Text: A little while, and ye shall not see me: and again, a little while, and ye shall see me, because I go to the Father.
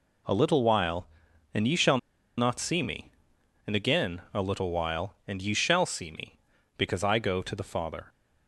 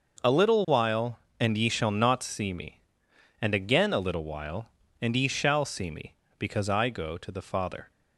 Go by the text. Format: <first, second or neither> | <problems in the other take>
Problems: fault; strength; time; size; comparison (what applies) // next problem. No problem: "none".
second | pauses between "shall" and "not"; at 1.9 s; 0.40 s long